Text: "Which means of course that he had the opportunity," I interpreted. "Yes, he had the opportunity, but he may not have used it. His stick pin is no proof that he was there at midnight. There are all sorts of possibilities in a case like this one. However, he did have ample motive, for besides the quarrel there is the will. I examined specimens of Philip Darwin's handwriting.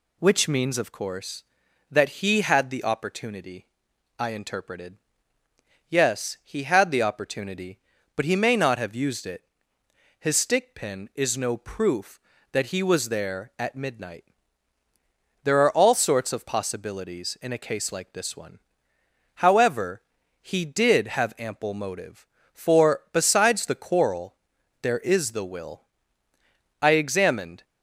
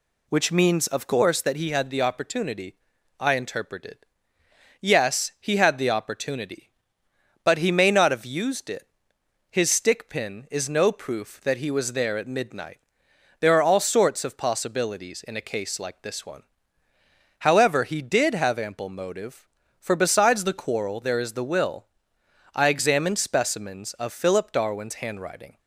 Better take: second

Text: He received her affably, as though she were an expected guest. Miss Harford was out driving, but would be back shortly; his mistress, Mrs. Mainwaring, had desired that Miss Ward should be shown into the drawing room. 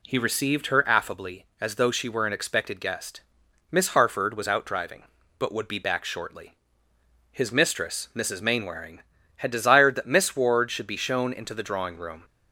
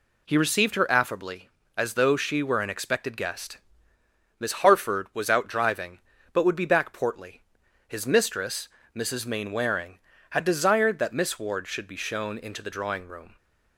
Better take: first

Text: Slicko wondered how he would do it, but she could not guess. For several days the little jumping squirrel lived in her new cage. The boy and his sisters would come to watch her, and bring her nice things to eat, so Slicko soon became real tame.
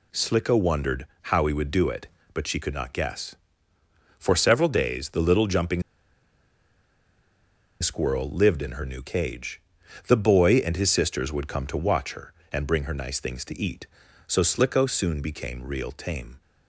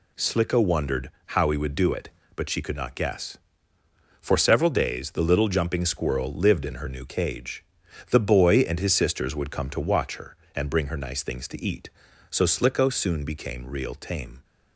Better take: second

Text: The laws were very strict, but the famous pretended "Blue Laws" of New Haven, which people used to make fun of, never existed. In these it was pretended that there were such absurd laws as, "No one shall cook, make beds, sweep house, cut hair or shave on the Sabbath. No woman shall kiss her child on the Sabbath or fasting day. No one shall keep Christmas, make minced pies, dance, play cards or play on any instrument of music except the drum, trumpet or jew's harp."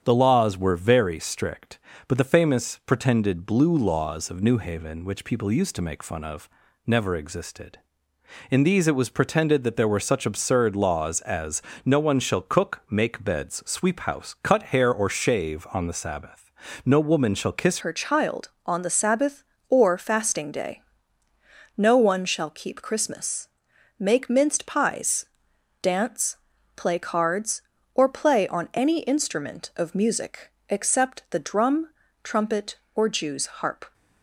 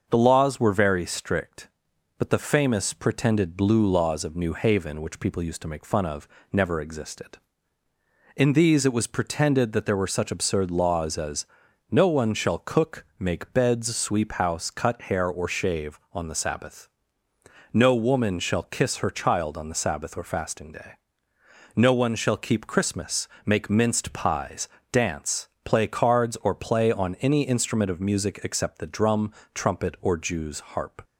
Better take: second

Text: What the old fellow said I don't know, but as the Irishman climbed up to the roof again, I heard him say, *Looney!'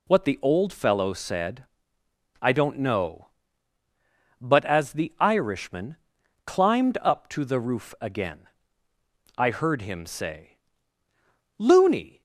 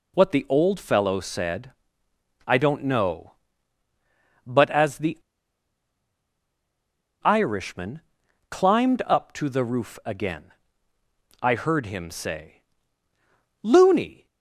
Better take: first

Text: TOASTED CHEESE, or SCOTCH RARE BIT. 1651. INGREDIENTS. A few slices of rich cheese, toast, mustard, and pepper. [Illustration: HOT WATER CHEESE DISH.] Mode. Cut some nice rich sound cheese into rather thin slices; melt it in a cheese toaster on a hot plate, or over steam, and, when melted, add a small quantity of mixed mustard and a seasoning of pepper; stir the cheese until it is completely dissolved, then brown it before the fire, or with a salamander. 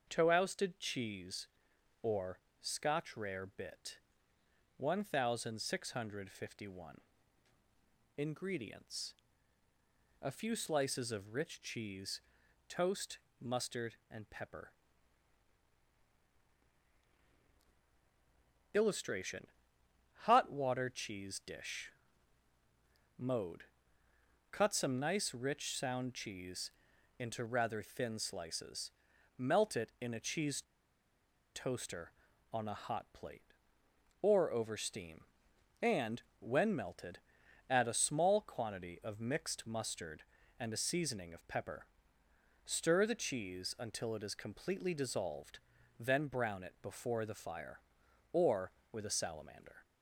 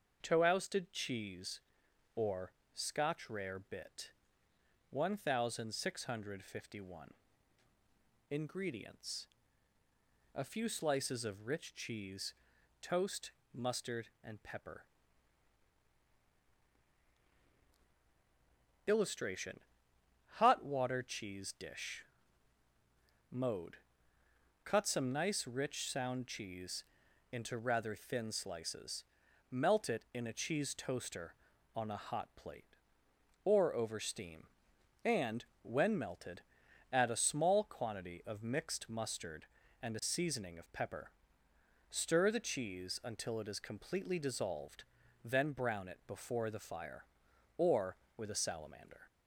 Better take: second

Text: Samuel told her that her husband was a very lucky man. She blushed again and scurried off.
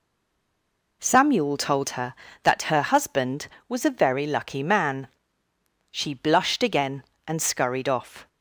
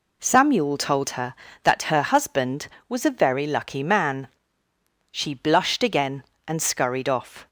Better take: second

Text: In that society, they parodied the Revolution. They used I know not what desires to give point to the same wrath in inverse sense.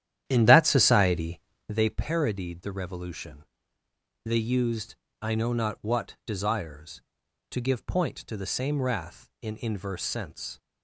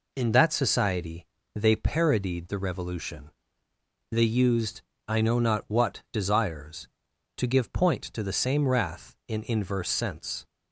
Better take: second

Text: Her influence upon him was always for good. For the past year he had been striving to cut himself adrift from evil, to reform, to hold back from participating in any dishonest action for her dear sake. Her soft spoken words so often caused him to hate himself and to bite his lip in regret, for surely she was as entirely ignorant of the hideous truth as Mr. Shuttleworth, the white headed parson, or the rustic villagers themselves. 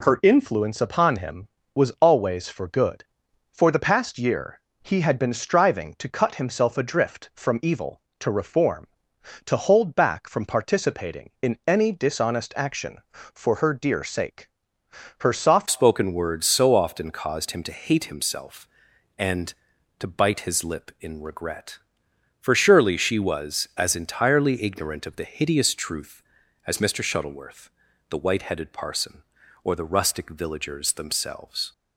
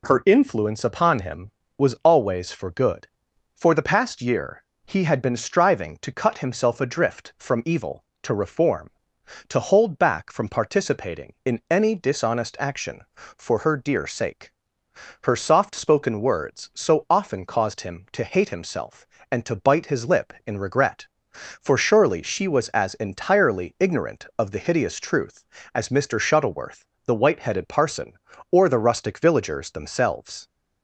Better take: second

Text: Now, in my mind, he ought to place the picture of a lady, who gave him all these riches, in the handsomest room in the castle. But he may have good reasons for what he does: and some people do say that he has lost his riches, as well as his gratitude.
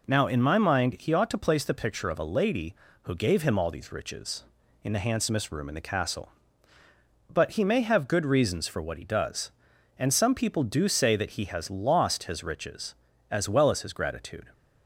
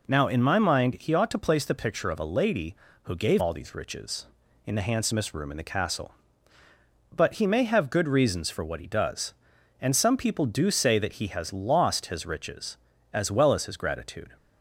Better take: first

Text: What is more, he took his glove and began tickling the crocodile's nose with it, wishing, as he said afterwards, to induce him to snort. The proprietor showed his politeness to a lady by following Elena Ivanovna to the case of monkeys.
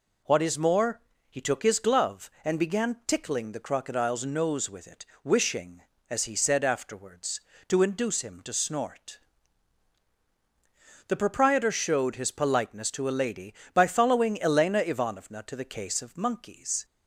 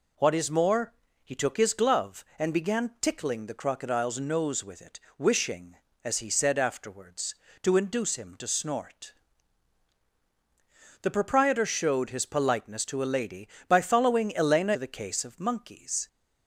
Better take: first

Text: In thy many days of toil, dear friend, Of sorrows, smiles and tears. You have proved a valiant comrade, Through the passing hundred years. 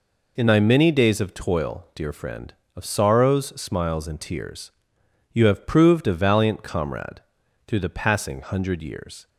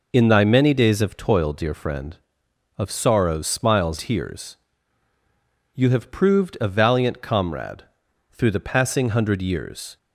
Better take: first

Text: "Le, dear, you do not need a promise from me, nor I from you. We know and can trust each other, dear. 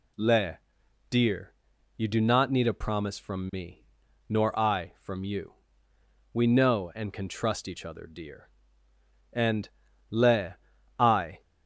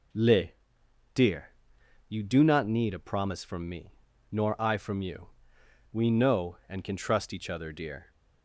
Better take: second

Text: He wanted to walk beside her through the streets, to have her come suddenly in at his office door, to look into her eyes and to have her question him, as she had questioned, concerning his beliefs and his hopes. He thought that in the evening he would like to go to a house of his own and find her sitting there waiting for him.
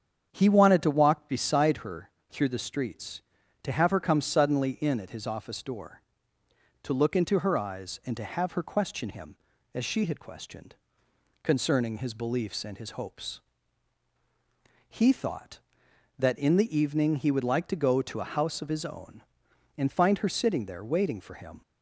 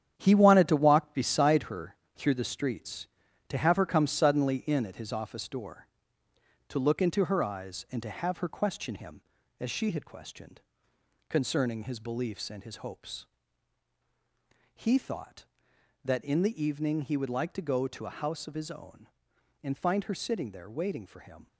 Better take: first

